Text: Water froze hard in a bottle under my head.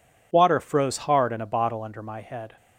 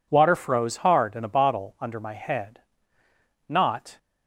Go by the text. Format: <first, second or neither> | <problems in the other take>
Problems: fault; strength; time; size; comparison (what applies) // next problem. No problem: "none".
first | goes on to say "Not"; from 3.4 s on; 0.50 s long